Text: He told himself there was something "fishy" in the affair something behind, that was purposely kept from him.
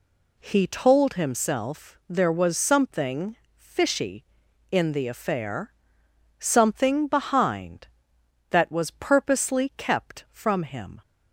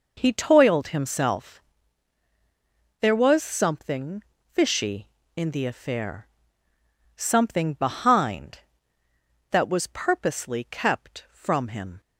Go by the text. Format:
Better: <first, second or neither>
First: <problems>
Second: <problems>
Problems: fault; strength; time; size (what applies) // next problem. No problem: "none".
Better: first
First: pauses between "something" and "fishy"; slight; at 3.3 s; 0.20 s long // pauses between "affair" and "something"; noticeable; at 5.7 s; 0.66 s long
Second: says "toiled" for "told"; at 0.3 s // pauses between "himself" and "there"; strong; at 1.6 s; 1.4 s long // pauses between "something" and "fishy"; slight; at 4.2 s; 0.28 s long // pauses between "affair" and "something"; noticeable; at 6.2 s; 0.90 s long